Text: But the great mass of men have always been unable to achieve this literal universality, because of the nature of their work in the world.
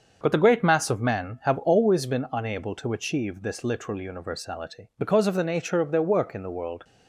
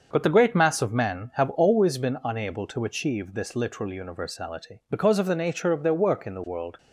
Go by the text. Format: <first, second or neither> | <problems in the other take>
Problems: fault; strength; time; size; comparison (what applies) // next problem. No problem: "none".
neither | starts louder than the rest; the same in both